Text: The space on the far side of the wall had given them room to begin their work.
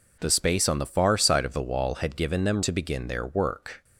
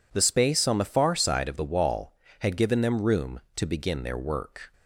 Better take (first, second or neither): second